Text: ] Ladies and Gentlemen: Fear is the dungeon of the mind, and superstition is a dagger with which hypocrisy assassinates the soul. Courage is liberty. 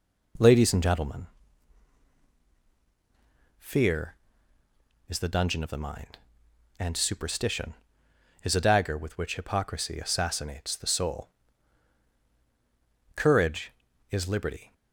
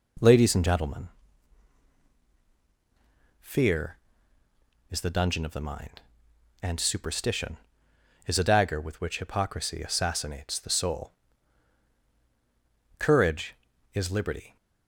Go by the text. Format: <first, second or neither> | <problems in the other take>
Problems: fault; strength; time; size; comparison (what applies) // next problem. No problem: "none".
neither | none